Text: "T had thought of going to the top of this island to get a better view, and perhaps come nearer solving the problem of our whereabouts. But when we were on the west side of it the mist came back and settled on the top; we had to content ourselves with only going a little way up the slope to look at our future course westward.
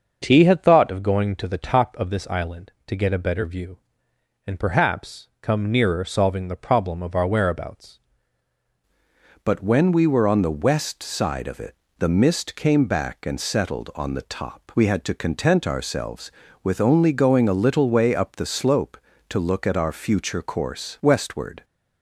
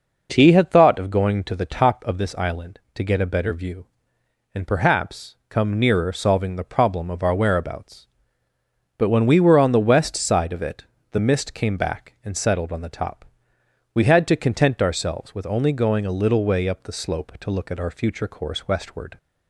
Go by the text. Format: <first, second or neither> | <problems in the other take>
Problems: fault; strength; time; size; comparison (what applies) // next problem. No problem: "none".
second | starts louder than the rest; until 1.2 s; 6.5 dB // changes voice at "But"; from 9.4 s on; 12.2 s long // pauses between "it" and "the"; slight; at 11.7 s; 0.24 s long; slight in the second